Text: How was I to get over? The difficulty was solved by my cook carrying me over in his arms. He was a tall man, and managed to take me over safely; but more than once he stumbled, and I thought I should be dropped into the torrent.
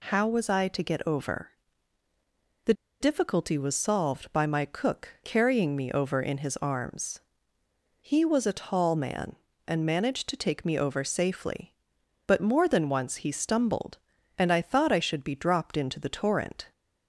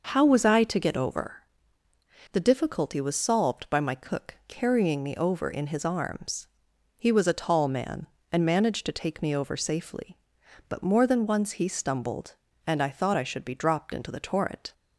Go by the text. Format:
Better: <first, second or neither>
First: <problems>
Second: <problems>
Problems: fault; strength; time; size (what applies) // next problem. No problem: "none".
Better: second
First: pauses between "The" and "difficulty"; slight; at 2.7 s; 0.27 s long // pauses between "cook" and "carrying"; slight; at 5.0 s; 0.16 s long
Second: none